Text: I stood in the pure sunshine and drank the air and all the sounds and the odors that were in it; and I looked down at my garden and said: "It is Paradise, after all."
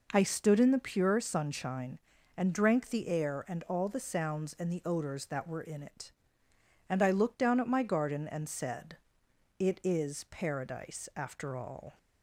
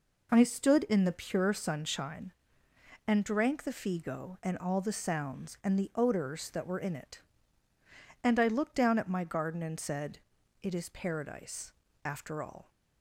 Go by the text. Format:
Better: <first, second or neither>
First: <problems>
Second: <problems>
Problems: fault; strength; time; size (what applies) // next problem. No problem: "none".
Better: first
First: none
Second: says "figo" for "air"; at 3.7 s